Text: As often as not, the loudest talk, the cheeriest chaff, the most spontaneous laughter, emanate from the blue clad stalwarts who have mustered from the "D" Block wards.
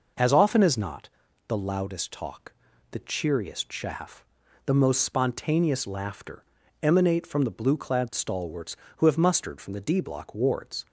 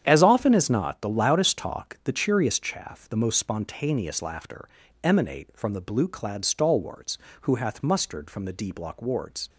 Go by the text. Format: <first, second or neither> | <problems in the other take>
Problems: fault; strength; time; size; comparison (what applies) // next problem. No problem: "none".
first | starts louder than the rest; strong; until 1.0 s; 9 dB // says "hath" for "have"; at 7.5 s